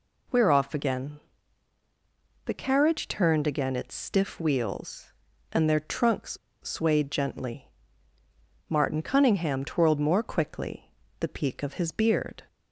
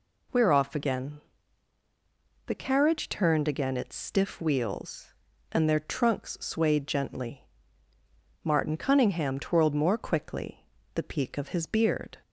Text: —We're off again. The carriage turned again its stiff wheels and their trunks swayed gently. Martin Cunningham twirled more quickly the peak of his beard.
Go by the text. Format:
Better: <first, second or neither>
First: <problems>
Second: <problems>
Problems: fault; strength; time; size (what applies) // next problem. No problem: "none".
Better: second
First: pauses between "trunks" and "swayed"; slight; at 6.3 s; 0.25 s long // pauses between "quickly" and "the"; slight; at 10.8 s; 0.30 s long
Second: pauses between "quickly" and "the"; slight; at 10.6 s; 0.30 s long